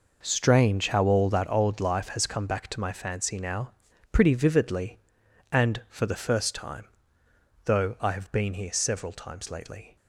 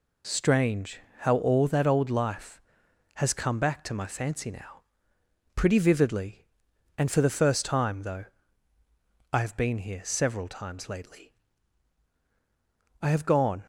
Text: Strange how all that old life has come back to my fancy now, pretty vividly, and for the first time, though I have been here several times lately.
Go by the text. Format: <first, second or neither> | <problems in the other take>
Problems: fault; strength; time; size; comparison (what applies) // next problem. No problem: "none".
first | pauses between "Strange" and "how"; slight; at 0.9 s; 0.22 s long // pauses between "though" and "I"; at 8.2 s; 1.0 s long // goes on to say "I have gone"; noticeable; from 12.9 s on; 0.66 s long